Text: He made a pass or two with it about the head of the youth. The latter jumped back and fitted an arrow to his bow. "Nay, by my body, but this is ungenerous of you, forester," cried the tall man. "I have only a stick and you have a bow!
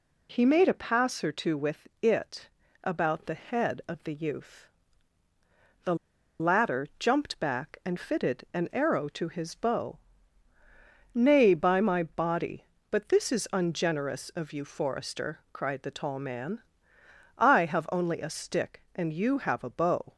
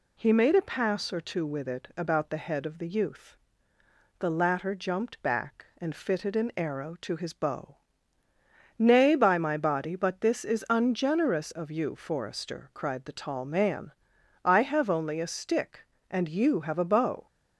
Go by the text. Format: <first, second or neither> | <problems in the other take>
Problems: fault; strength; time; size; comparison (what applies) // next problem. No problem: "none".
second | pauses between "it" and "about"; slight; at 2.4 s; 0.36 s long // pauses between "The" and "latter"; at 5.9 s; 0.45 s long